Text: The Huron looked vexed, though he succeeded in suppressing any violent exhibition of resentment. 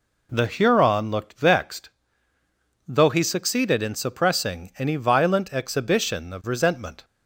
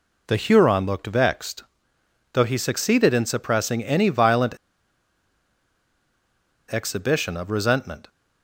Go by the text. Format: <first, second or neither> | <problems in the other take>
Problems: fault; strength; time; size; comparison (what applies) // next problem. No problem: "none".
first | pauses between "violent" and "exhibition"; strong; at 4.5 s; 2.1 s long